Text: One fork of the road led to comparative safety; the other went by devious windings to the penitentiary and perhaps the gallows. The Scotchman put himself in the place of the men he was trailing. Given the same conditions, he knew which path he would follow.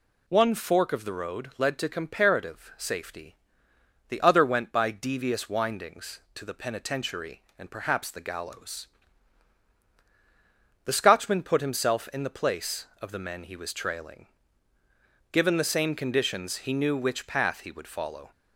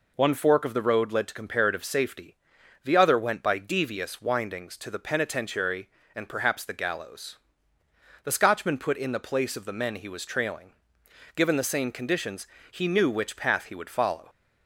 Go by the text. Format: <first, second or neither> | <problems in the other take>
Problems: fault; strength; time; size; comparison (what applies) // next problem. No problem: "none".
first | skips "himself"; at 8.9 s